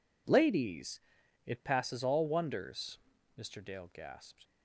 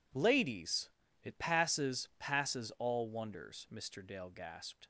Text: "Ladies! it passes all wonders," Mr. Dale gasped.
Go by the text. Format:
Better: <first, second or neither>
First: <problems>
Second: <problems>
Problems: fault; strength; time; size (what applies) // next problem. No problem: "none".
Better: first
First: none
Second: says "passes" twice; at 2.1 s